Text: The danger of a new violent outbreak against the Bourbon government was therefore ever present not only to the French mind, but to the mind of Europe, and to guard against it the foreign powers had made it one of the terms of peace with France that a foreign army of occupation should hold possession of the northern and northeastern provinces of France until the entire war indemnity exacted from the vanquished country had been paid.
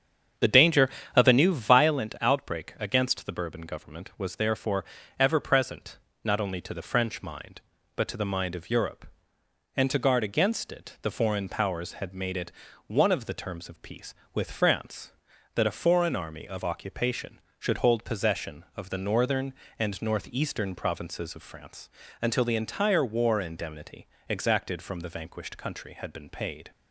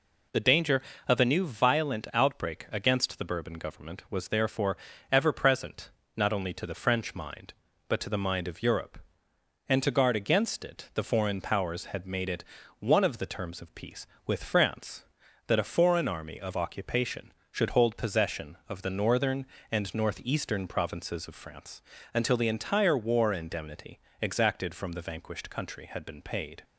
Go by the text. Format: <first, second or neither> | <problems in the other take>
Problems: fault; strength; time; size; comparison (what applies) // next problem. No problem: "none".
second | starts louder than the rest; strong; until 2.0 s; 7.5 dB // pauses between "therefore" and "ever"; slight; at 4.8 s; 0.34 s long; slight in the second // pauses between "present" and "not"; slight; at 5.9 s; 0.26 s long; slight in the second // pauses between "it" and "one"; slight; at 12.5 s; 0.36 s long; slight in the second // pauses between "France" and "until"; slight; at 21.8 s; 0.32 s long; slight in the second // pauses between "indemnity" and "exacted"; slight; at 24.0 s; 0.24 s long; slight in the second